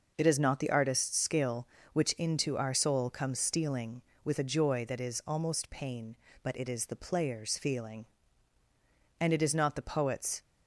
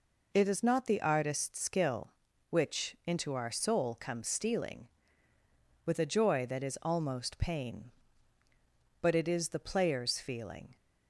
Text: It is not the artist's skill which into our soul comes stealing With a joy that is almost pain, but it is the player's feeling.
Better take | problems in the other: second | goes on to say "And it is not the poet's"; noticeable; from 9.1 s on; 1.2 s long

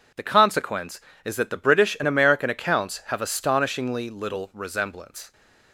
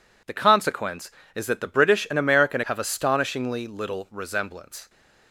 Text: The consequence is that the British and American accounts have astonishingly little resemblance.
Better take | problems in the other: first | skips "accounts"; at 2.6 s

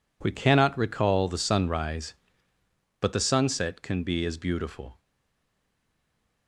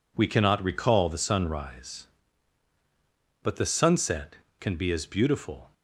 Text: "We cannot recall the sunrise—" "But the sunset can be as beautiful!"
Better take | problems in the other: second | stays silent after the last word; noticeable; from 4.9 s on; 1.5 s long

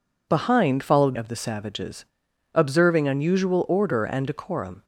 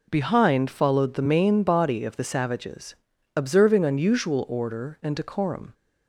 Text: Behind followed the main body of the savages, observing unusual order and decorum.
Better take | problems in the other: second | skips "the main body"; at 1.1 s

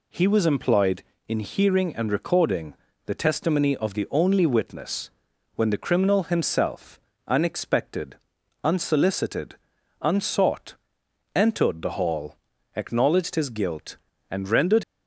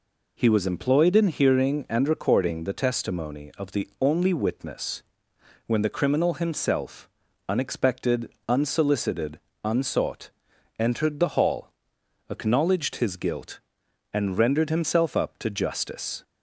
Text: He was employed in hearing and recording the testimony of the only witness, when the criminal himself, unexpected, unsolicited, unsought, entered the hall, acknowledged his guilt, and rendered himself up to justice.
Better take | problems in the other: second | pauses between "recording" and "the"; slight; at 2.7 s; 0.32 s long // stops before "himself up to justice"; at 14.8 s

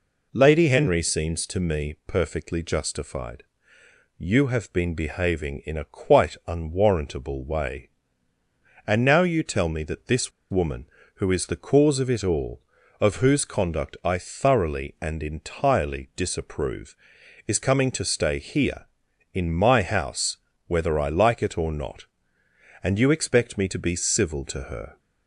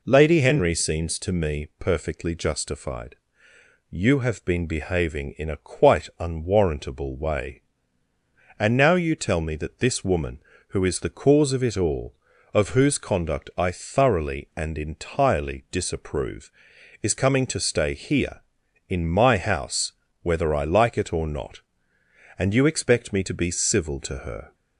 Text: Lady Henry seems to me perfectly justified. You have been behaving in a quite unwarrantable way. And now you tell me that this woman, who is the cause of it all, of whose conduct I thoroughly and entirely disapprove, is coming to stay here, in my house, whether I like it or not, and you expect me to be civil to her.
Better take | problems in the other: second | pauses between "this" and "woman"; slight; at 10.3 s; 0.19 s long

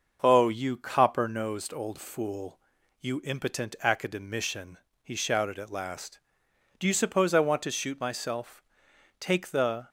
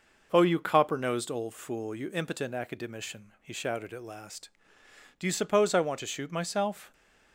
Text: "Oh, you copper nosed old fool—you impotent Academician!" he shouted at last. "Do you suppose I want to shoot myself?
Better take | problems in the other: second | starts louder than the rest; until 1.2 s; 6.5 dB // goes on to say "Take the"; noticeable; from 9.1 s on; 0.70 s long

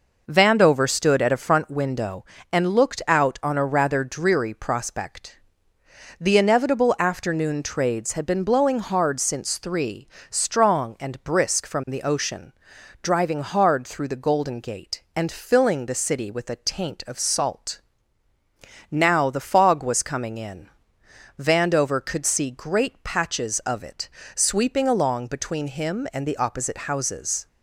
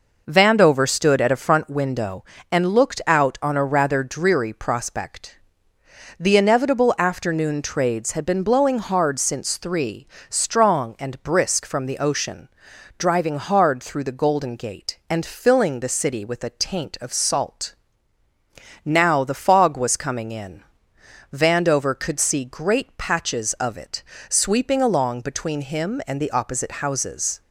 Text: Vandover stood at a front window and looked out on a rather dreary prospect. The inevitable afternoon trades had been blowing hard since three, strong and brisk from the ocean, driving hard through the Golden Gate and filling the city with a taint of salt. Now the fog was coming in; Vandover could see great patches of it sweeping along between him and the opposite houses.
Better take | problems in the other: neither | pauses between "it" and "sweeping"; slight; the same in both

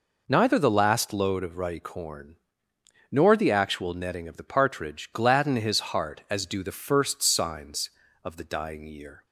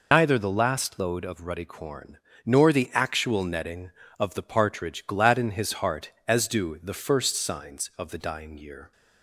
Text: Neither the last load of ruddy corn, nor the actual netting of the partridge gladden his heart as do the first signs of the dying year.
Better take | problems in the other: first | loses the start of "Neither"; at 0.1 s; 105 ms

